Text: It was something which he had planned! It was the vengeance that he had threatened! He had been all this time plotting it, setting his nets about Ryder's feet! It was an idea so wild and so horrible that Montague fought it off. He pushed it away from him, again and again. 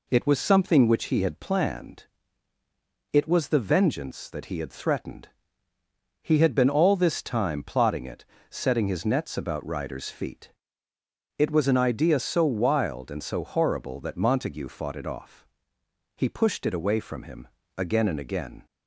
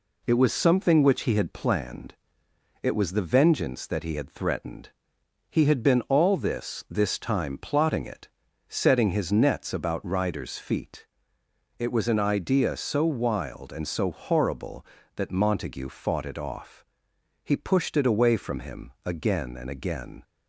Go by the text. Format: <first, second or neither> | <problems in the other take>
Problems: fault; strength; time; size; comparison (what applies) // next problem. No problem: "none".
first | says "this" twice; at 6.8 s